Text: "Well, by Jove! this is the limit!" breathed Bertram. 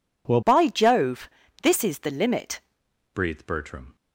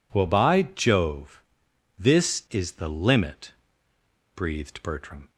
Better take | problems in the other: second | changes voice from "by" to "limit"; from 0.4 to 2.6 s; 2.2 s long

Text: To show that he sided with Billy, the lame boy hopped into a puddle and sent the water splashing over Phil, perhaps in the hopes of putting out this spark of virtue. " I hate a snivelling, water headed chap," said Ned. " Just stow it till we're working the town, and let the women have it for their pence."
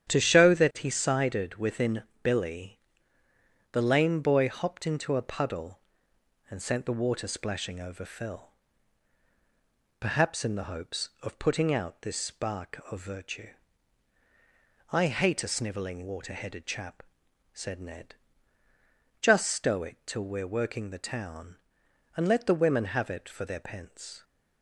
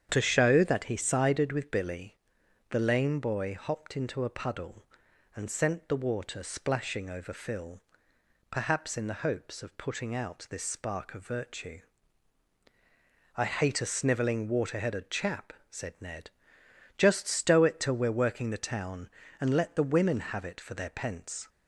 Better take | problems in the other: second | starts louder than the rest; strong; until 1.1 s; 9.5 dB; strong in the second // says "within" for "with"; at 1.5 s

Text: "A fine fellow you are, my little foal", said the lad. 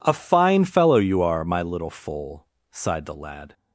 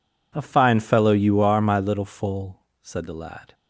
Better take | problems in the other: second | says "sighed" for "said"; at 2.7 s

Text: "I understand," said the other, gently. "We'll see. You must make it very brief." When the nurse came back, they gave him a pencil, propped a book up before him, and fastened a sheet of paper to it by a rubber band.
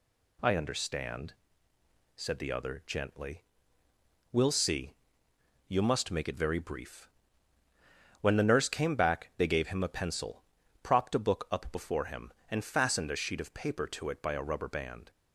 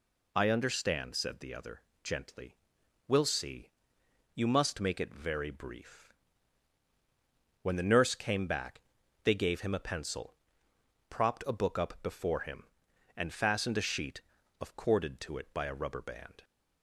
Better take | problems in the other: first | says "corded" for "paper"; at 14.7 s

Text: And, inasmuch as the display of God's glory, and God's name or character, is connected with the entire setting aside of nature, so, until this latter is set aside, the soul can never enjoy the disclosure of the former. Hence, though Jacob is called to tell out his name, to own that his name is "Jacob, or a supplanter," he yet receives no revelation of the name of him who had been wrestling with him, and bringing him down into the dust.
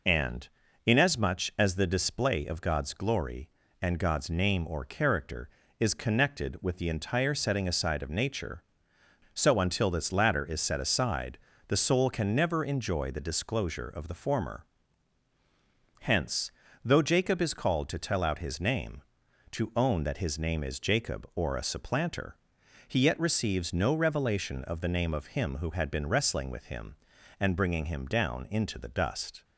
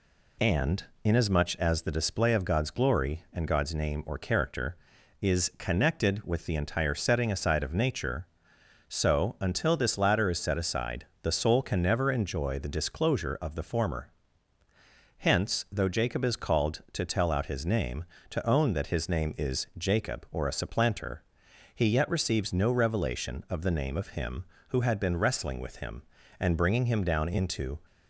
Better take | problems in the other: first | stops before "the dust"; at 27.8 s

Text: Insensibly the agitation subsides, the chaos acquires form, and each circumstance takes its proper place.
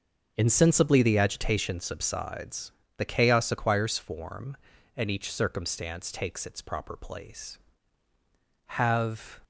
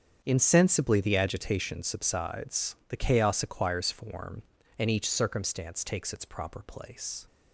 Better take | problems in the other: second | starts louder than the rest; until 1.3 s; 6.5 dB; strong in the second // goes on to say "Have"; noticeable; from 8.6 s on; 0.72 s long

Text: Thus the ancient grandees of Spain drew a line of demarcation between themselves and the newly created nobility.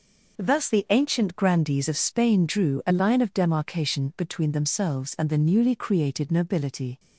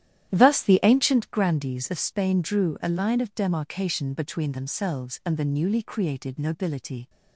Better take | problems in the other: first | starts louder than the rest; strong; until 1.4 s; 11.5 dB

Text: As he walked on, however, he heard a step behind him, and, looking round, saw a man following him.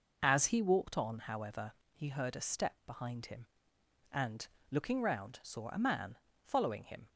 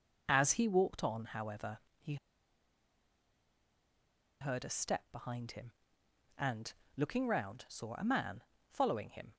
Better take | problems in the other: first | pauses between "he" and "heard"; strong; at 2.1 s; 2.2 s long // pauses between "man" and "following"; slight; at 8.4 s; 0.28 s long; slight in the first

